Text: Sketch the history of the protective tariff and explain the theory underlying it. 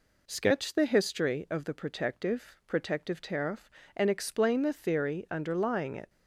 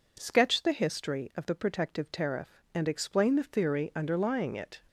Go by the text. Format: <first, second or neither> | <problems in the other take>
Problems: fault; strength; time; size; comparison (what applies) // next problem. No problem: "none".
second | says "protective" twice; at 2.6 s